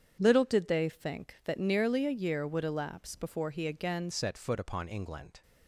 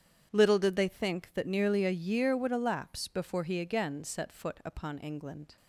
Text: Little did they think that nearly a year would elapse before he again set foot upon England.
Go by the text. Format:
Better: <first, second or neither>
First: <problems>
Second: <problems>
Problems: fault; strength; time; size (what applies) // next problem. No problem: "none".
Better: second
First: starts louder than the rest; strong; until 1.2 s; 8 dB // changes voice at "set"; from 4.1 s on; 1.3 s long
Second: starts louder than the rest; strong; until 1.3 s; 8.5 dB